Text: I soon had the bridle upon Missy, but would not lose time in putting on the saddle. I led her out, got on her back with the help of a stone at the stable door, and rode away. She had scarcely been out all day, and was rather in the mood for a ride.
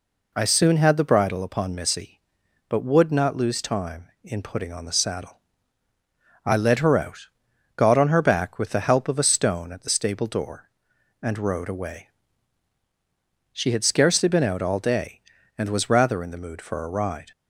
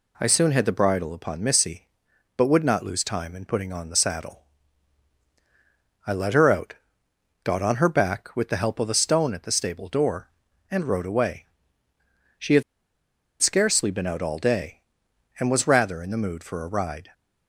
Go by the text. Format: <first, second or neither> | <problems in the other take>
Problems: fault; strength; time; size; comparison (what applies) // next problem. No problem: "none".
first | pauses between "had" and "scarcely"; noticeable; at 12.6 s; 0.79 s long